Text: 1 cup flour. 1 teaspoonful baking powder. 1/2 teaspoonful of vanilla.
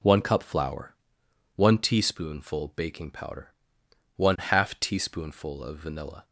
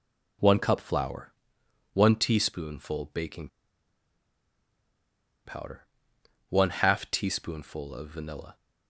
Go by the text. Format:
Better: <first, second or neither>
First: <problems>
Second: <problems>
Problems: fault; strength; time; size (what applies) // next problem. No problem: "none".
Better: first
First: none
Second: pauses between "baking" and "powder"; strong; at 3.4 s; 1.9 s long